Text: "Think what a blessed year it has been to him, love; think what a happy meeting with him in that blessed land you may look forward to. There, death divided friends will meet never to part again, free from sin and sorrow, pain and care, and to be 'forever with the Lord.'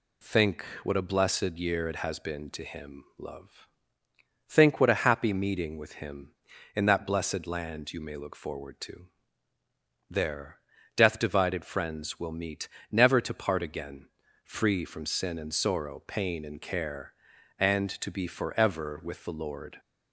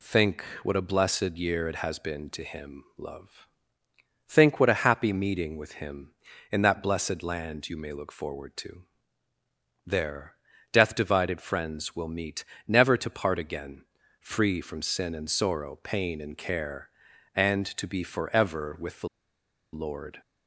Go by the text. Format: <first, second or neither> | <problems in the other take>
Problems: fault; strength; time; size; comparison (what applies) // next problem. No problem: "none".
first | pauses between "Think" and "what"; slight; at 0.4 s; 0.20 s long; slight in the first // pauses between "meet" and "never"; slight; at 12.4 s; 0.22 s long; slight in the first // pauses between "the" and "Lord"; noticeable; at 19.0 s; 0.66 s long